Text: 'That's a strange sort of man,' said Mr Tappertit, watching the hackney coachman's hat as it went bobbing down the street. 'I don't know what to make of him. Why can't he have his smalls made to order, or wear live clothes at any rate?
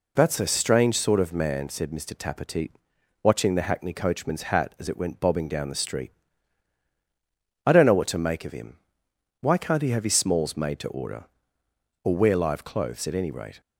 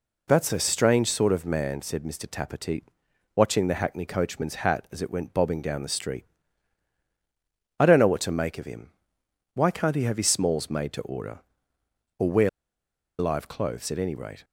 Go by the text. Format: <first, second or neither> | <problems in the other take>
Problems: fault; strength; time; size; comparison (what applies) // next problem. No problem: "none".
first | pauses between "wear" and "live"; noticeable; at 12.4 s; 0.70 s long